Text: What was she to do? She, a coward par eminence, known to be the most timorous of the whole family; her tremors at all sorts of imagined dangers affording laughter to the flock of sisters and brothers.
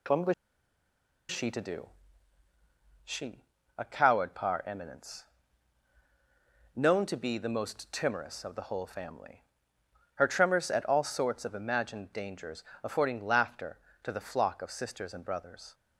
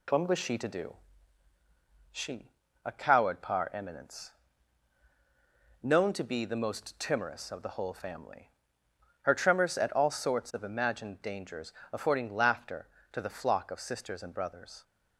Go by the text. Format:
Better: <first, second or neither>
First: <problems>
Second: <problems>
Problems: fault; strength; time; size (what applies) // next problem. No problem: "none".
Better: second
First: pauses between "was" and "she"; noticeable; at 0.3 s; 0.97 s long // pauses between "dangers" and "affording"; slight; at 12.6 s; 0.22 s long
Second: pauses between "dangers" and "affording"; slight; at 11.7 s; 0.22 s long